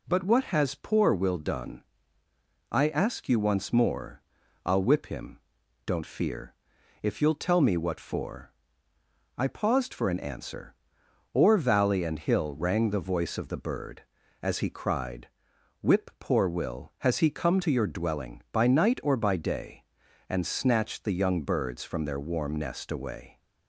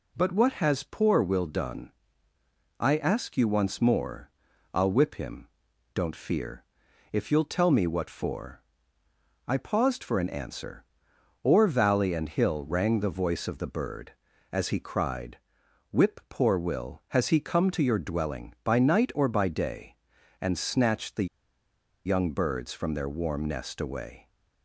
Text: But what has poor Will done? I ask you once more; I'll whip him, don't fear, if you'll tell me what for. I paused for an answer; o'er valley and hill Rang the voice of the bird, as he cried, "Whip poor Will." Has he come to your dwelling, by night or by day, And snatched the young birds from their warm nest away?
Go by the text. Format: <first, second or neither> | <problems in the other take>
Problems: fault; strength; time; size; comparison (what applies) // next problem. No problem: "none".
first | pauses between "the" and "young"; noticeable; at 21.2 s; 0.79 s long